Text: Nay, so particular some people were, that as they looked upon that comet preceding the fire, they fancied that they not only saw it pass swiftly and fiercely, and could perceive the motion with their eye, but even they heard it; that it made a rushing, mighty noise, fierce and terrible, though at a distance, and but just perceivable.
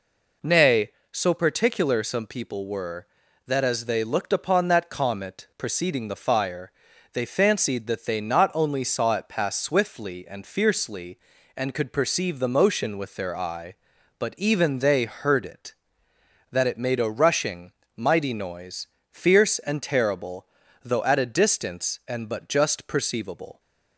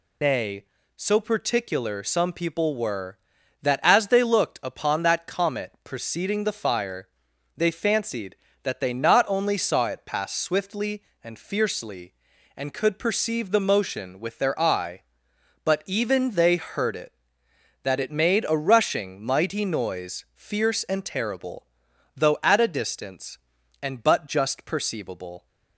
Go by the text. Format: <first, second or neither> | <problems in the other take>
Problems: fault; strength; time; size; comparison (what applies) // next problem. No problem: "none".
first | loses the start of "Nay"; at 0.2 s; 130 ms